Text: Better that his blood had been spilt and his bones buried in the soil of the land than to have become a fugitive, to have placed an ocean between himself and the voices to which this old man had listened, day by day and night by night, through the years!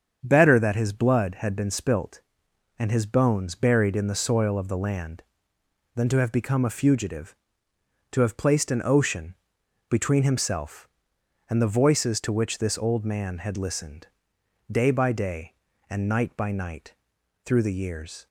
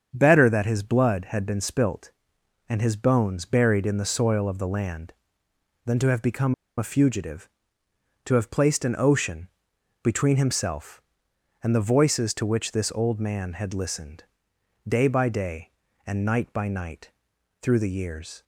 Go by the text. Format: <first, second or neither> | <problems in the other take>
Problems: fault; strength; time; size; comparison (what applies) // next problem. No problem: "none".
first | starts louder than the rest; strong; until 1.1 s; 7.5 dB; strong in the first // pauses between "become" and "a"; slight; at 6.5 s; 0.23 s long // pauses between "ocean" and "between"; noticeable; at 9.4 s; 0.56 s long; noticeable in the first